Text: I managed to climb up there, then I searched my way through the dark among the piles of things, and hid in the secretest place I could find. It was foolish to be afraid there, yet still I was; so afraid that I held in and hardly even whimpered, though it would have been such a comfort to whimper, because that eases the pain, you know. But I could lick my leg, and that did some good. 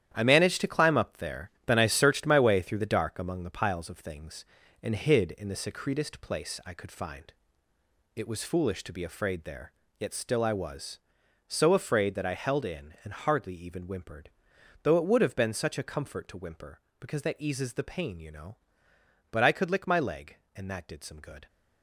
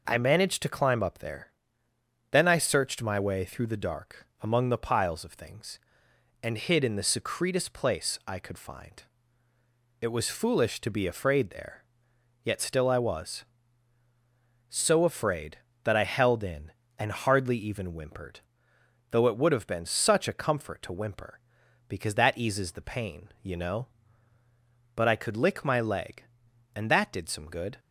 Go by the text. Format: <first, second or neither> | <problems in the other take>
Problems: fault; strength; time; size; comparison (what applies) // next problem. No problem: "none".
second | gets quieter; strong; throughout; 9 dB